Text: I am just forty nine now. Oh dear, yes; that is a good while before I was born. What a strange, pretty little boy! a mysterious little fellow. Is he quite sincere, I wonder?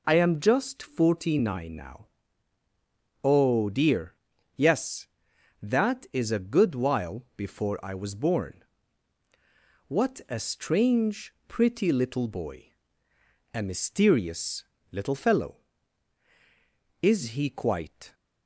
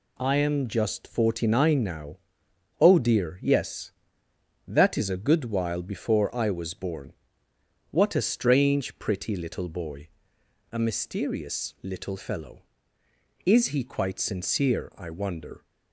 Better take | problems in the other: second | pauses between "mysterious" and "little"; slight; at 14.6 s; 0.26 s long // stops before "sincere I wonder"; at 18.1 s

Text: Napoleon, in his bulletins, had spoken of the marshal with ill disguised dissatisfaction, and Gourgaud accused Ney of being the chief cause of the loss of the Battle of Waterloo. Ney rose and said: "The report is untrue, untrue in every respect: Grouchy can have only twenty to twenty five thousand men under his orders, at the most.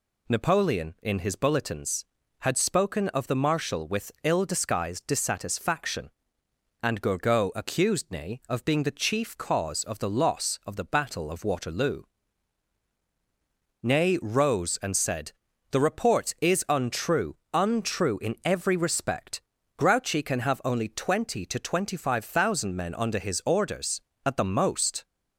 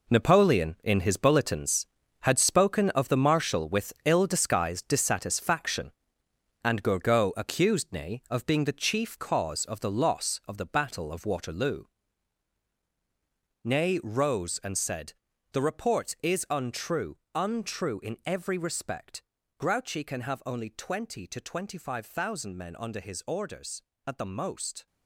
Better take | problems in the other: first | gets quieter; strong; throughout; 10.5 dB

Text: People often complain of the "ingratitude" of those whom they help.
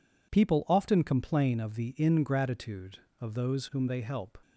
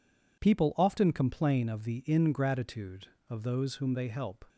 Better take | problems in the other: neither | none

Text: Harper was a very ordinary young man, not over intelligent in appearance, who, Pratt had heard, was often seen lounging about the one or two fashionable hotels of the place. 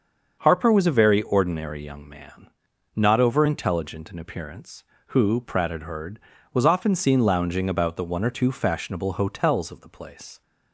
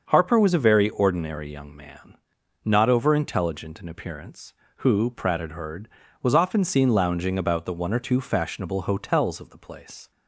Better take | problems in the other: neither | starts louder than the rest; the same in both

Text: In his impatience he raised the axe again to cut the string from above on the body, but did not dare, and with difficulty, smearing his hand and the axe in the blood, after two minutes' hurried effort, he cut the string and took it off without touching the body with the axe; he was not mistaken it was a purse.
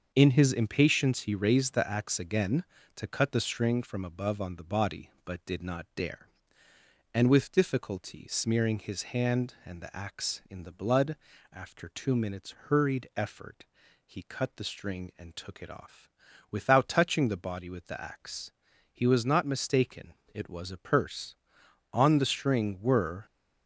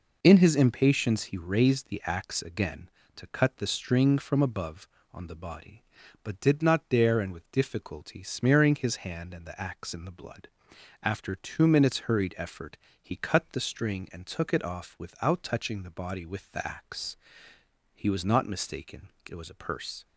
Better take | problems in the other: second | starts louder than the rest; until 1.1 s; 6.5 dB // pauses between "off" and "without"; at 16.0 s; 0.40 s long // pauses between "mistaken" and "it"; slight; at 20.1 s; 0.20 s long; slight in the second // goes on to say "On the string were"; from 21.9 s on; 1.3 s long

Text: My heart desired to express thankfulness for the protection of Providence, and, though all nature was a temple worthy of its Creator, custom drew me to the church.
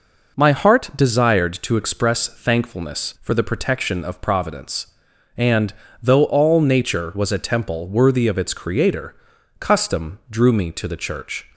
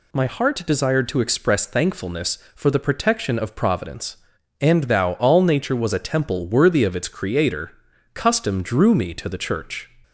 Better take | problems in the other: first | says "thou" for "though"; at 4.8 s

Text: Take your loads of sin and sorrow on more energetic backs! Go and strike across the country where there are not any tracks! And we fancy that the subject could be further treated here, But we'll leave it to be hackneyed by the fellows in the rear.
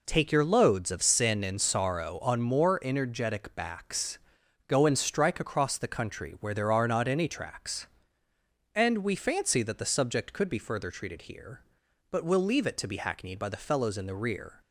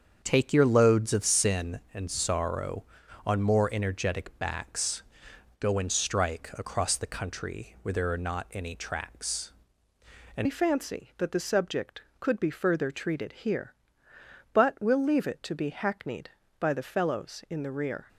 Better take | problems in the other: first | starts louder than the rest; strong; until 1.2 s; 7.5 dB // changes voice at "we"; from 10.4 s on; 7.6 s long

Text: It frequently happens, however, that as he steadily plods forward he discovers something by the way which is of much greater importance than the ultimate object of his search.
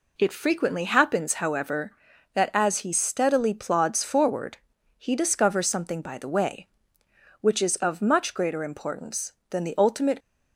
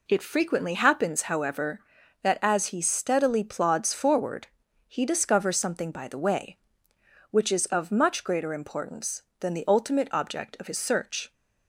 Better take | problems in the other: second | pauses between "forward" and "he"; at 4.5 s; 0.40 s long; also in the second // stops before "object of his search"; at 10.1 s

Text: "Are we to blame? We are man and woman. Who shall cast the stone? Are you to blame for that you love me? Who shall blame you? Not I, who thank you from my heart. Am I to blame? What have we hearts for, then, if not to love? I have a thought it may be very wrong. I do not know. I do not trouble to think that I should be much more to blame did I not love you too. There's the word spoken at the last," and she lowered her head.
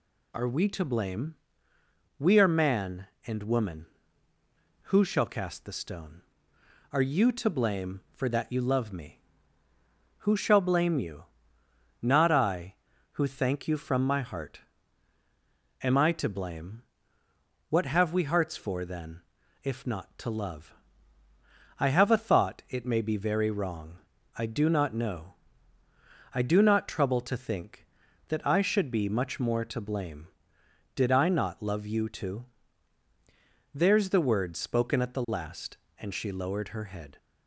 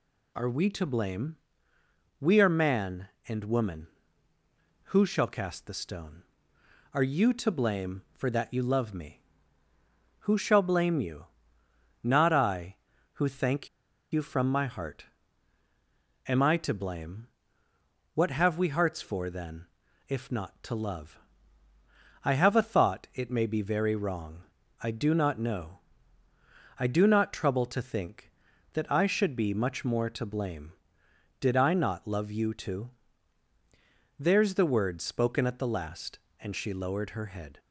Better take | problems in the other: first | pauses between "thank" and "you"; at 13.6 s; 0.44 s long

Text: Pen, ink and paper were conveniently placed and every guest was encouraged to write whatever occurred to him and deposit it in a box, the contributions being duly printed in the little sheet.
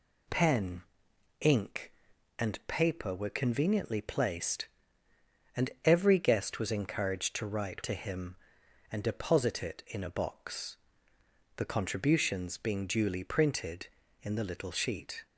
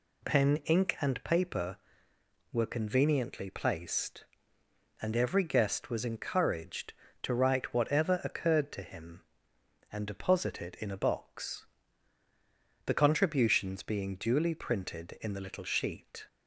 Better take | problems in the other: second | skips "whatever occurred"; at 7.8 s

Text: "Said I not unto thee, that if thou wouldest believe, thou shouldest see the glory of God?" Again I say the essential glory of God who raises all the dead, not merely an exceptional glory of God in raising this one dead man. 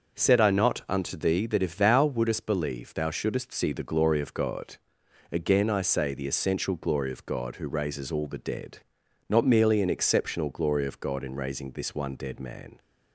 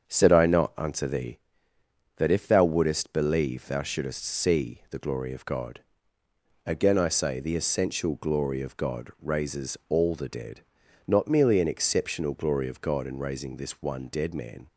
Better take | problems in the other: first | starts louder than the rest; strong; until 1.1 s; 7 dB; also in the first // skips "who"; at 9.1 s

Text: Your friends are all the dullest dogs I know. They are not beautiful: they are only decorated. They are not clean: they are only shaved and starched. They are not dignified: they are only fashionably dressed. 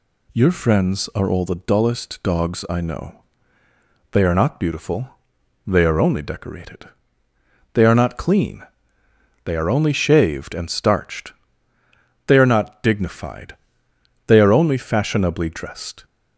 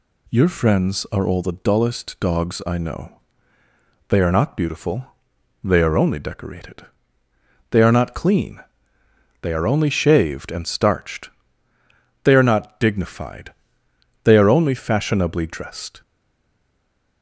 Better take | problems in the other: first | stays silent after the last word; noticeable; from 16.0 s on; 1.2 s long

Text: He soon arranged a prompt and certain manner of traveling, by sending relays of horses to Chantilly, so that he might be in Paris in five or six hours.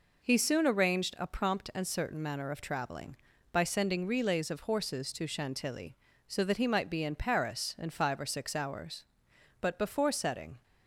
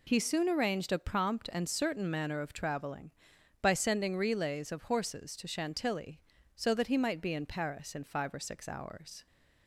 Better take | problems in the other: second | goes on to say "But before setting"; noticeable; from 9.6 s on; 1.0 s long

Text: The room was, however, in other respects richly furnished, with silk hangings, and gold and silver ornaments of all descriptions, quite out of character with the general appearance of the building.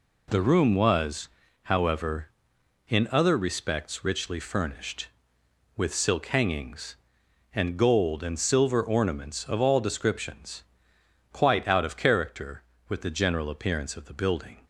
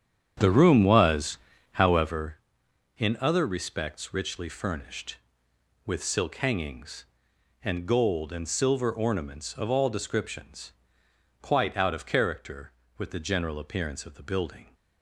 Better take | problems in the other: first | starts louder than the rest; strong; until 2.2 s; 8.5 dB

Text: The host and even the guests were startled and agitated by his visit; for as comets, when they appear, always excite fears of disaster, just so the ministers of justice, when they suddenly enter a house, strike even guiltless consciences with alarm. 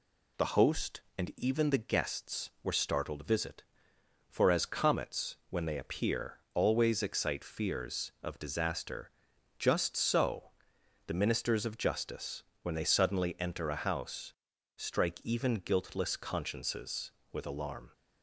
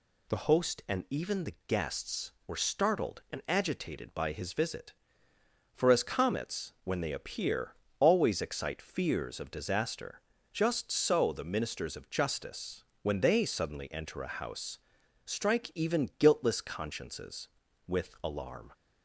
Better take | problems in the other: second | skips "and agitated by his"; at 3.2 s // pauses between "so" and "the"; noticeable; at 10.5 s; 0.56 s long

